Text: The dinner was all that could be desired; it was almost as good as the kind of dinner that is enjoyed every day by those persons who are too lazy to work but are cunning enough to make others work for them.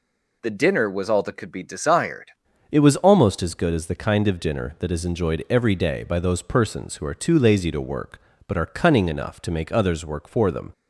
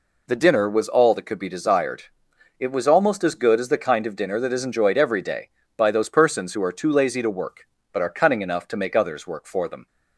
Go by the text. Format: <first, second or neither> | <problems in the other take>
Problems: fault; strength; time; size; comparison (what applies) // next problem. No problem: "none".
second | changes voice at "it"; from 2.7 s on; 8.0 s long